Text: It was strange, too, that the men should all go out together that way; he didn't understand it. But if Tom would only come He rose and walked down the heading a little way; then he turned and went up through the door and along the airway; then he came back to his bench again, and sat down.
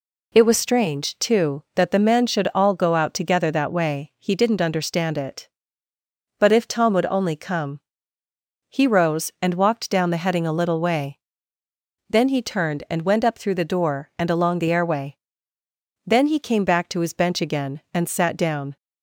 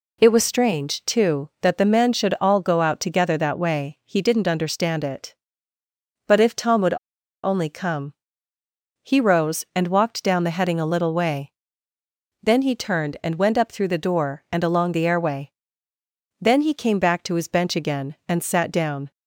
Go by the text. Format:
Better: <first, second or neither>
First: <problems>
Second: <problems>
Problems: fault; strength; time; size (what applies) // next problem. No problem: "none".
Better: first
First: pauses between "come" and "He"; noticeable; at 7.8 s; 0.88 s long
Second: pauses between "would" and "only"; noticeable; at 6.9 s; 0.50 s long // pauses between "come" and "He"; noticeable; at 8.1 s; 0.88 s long